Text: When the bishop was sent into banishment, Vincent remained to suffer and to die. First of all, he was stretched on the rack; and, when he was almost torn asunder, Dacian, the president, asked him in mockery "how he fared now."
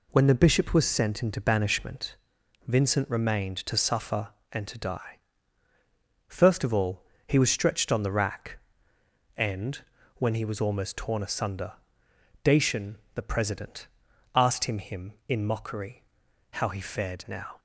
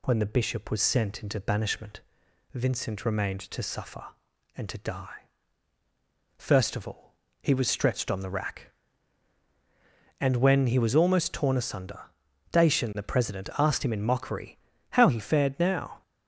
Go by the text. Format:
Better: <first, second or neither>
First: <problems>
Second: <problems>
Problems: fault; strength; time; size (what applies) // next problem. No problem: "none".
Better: second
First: says "him" twice; at 14.7 s // pauses between "mockery" and "how"; noticeable; at 16.0 s; 0.46 s long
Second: pauses between "mockery" and "how"; slight; at 14.5 s; 0.32 s long